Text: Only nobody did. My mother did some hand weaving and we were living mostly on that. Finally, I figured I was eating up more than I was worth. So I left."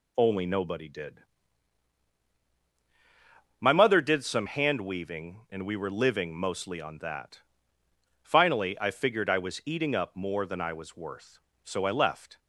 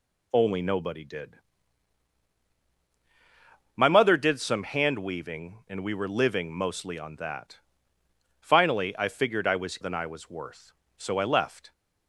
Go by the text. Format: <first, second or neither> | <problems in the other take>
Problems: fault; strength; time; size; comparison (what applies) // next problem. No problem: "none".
first | skips "eating up more"; at 9.7 s